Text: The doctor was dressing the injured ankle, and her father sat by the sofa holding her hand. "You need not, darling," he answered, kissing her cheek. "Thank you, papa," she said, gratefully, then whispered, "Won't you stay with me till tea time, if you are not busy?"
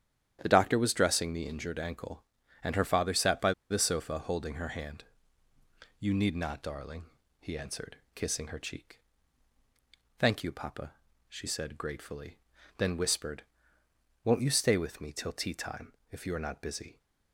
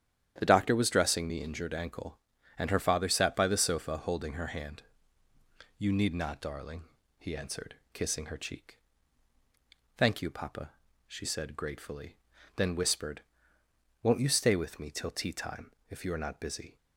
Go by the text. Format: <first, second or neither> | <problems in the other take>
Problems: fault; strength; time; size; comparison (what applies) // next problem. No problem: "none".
second | starts louder than the rest; strong; until 1.4 s; 10 dB; strong in the second // pauses between "by" and "the"; slight; at 3.5 s; 0.18 s long